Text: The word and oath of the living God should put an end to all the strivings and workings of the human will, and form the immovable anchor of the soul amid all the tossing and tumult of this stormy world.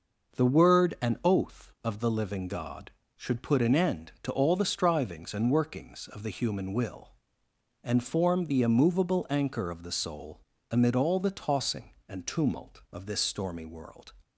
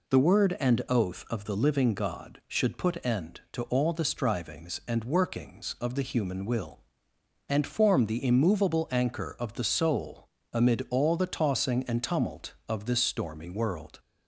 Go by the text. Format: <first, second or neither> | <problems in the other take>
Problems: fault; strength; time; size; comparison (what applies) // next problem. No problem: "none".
first | skips "an"; at 3.0 s // pauses between "soul" and "amid"; slight; at 10.2 s; 0.24 s long; slight in the first